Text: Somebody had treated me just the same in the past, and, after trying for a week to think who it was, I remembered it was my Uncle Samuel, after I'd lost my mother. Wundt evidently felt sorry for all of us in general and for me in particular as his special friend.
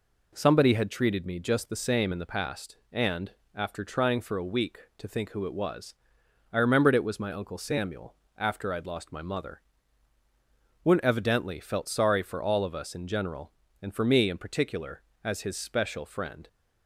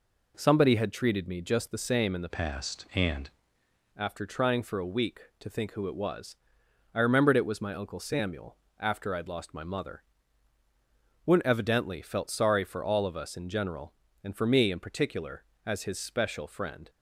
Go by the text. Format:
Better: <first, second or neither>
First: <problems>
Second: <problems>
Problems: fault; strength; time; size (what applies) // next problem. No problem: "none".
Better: first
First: none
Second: changes voice from "past" to "and"; from 2.3 to 3.3 s; 1.0 s long